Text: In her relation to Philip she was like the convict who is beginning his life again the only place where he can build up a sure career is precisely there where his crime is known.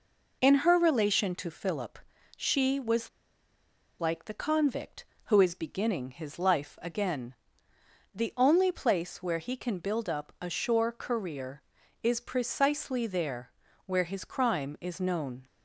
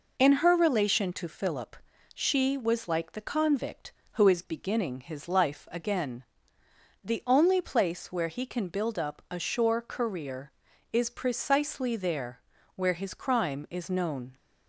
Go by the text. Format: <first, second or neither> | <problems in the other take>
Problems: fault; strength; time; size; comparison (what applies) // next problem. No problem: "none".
second | pauses between "Philip" and "she"; at 1.9 s; 0.38 s long; also in the second // pauses between "was" and "like"; noticeable; at 3.0 s; 0.91 s long // pauses between "again" and "the"; noticeable; at 7.3 s; 0.80 s long; noticeable in the second // pauses between "there" and "where"; slight; at 13.5 s; 0.36 s long; slight in the second